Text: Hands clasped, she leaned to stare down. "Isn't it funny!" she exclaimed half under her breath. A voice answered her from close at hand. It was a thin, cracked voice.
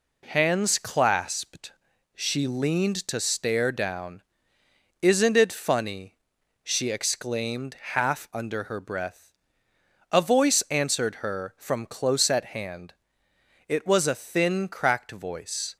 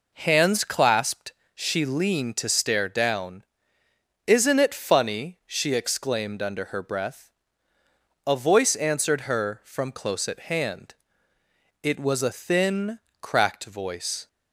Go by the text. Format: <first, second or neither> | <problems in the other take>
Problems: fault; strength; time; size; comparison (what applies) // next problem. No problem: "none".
first | skips "half"; at 6.3 s